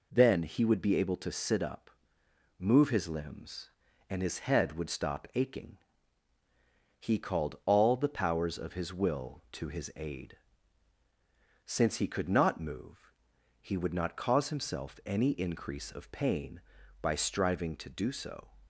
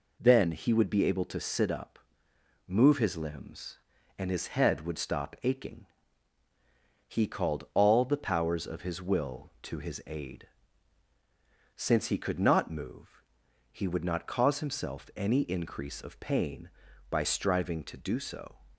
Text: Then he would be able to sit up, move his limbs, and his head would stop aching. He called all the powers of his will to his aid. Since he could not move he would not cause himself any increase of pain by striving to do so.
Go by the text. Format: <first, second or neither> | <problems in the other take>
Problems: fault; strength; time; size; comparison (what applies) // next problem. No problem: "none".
neither | pauses between "move" and "he"; noticeable; the same in both